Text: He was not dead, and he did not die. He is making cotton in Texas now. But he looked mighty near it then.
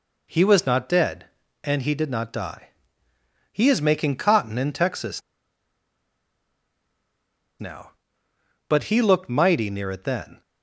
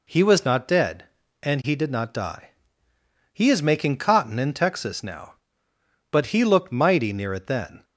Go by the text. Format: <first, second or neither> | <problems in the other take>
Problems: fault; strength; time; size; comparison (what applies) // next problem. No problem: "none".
second | pauses between "Texas" and "now"; strong; at 5.2 s; 2.4 s long